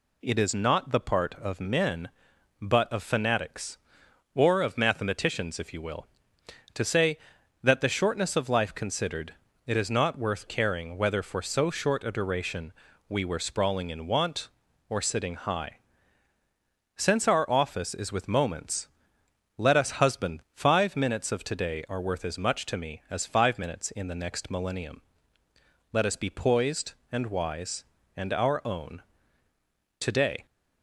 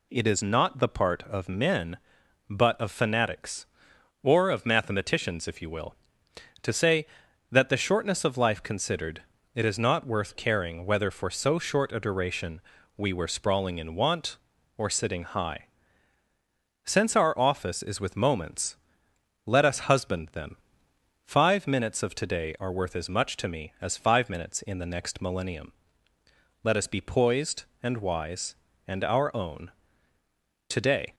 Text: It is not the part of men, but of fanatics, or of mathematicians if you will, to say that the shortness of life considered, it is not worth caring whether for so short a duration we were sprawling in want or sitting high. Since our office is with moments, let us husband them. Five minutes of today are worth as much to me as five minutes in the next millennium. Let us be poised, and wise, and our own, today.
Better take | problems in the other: second | pauses between "duration" and "we"; slight; at 12.7 s; 0.36 s long; slight in the second // skips "them"; at 20.4 s

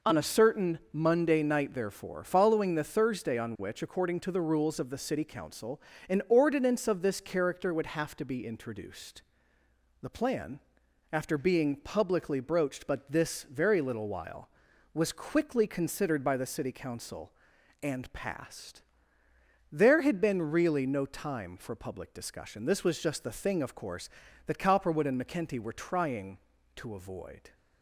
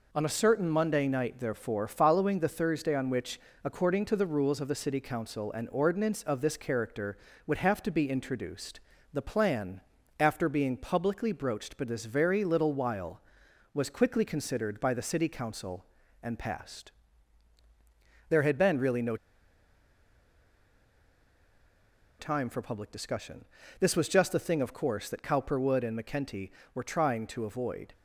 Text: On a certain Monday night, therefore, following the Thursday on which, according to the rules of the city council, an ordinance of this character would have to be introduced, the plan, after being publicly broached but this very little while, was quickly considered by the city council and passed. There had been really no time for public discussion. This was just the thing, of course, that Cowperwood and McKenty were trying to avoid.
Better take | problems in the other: first | pauses between "no" and "time"; strong; at 19.1 s; 3.0 s long

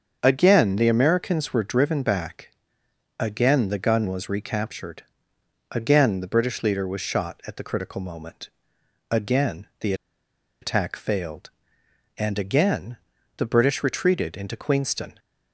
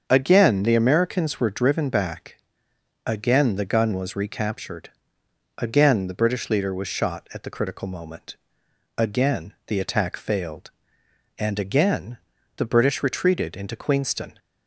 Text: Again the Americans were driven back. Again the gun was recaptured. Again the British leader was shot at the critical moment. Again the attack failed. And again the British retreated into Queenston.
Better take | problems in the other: second | starts louder than the rest; until 1.2 s; 7 dB; also in the second // pauses between "the" and "attack"; noticeable; at 9.9 s; 0.68 s long // pauses between "again" and "the"; at 12.9 s; 0.38 s long; also in the second

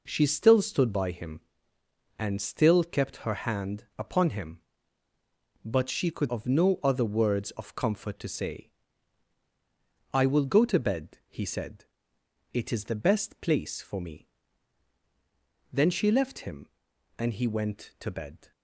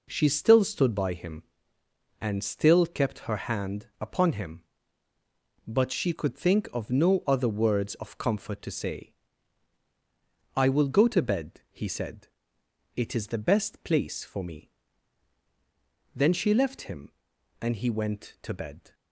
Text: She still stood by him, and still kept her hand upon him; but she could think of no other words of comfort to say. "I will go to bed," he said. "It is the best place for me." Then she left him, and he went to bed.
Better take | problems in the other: second | skips "think"; at 6.2 s

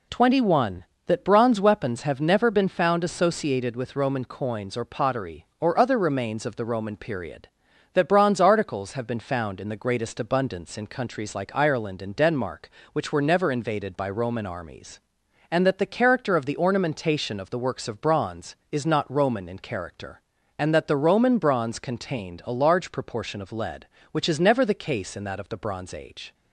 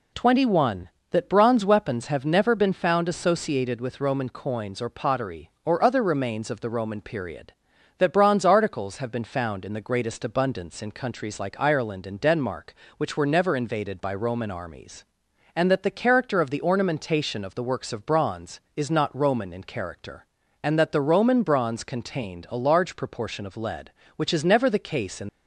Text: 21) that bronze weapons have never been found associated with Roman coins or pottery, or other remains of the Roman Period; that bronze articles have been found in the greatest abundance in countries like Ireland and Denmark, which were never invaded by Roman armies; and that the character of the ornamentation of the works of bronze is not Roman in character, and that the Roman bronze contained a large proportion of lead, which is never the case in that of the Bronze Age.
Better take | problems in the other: first | stops before "that of the Bronze Age"; at 25.2 s

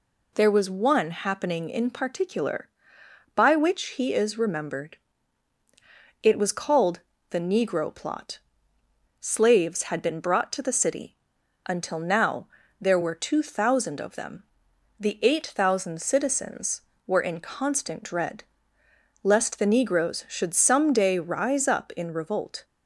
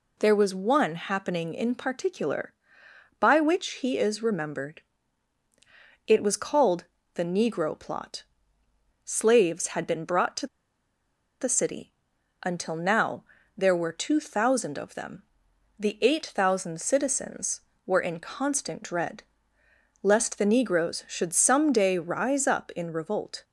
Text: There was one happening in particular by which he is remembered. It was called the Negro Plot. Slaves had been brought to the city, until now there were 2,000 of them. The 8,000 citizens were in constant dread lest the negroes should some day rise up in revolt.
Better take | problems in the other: first | pauses between "called" and "the"; slight; at 6.8 s; 0.30 s long; slight in the first // pauses between "to" and "the"; noticeable; at 10.4 s; 0.95 s long // pauses between "now" and "there"; slight; at 13.2 s; 0.32 s long; slight in the first // pauses between "dread" and "lest"; noticeable; at 19.2 s; 0.78 s long; noticeable in the first

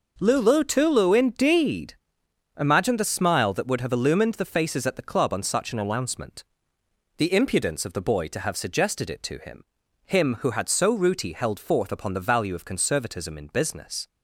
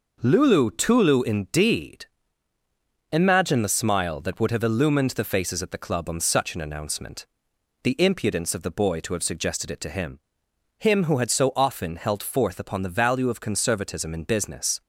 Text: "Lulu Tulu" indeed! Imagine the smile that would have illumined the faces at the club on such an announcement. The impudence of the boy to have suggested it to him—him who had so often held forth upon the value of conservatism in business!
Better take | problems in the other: second | says "rooty" for "often"; at 10.9 s

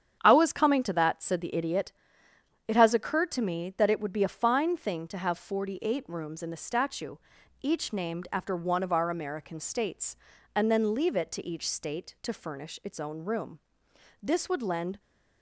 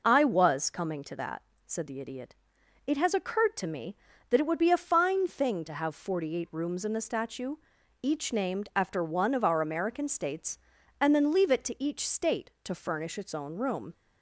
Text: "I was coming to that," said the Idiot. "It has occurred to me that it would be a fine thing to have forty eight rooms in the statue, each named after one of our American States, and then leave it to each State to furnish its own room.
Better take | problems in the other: second | starts louder than the rest; strong; until 1.2 s; 8.5 dB // goes on to say "This would lend"; noticeable; from 14.2 s on; 0.78 s long

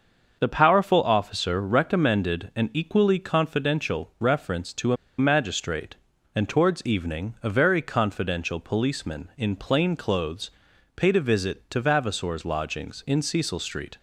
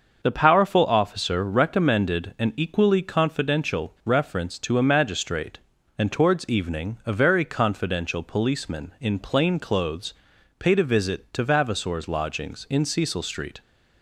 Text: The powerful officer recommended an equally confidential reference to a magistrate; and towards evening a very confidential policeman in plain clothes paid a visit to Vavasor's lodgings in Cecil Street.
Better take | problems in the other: second | starts louder than the rest; until 1.4 s; 6.5 dB; also in the second // pauses between "a" and "magistrate"; slight; at 4.9 s; 0.24 s long // pauses between "clothes" and "paid"; at 10.5 s; 0.42 s long; also in the second

